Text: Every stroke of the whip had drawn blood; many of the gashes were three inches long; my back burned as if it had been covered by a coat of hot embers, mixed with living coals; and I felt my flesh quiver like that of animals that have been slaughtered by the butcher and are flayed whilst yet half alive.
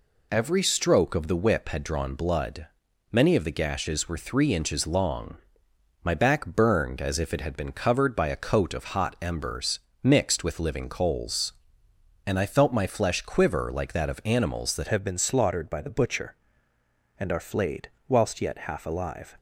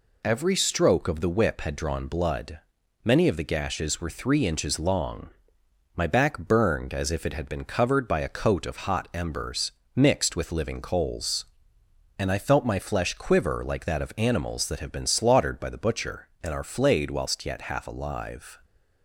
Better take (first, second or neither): second